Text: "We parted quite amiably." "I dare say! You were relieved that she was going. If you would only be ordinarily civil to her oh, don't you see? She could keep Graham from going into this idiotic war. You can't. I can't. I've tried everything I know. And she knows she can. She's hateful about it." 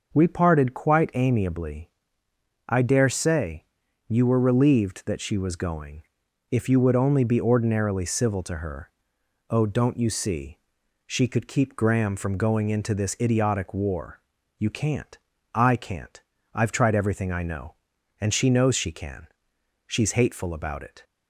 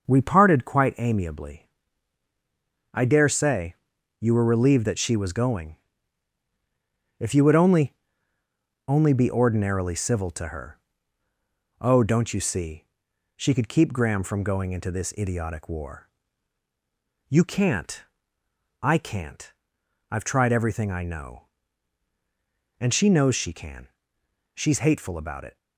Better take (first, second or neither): first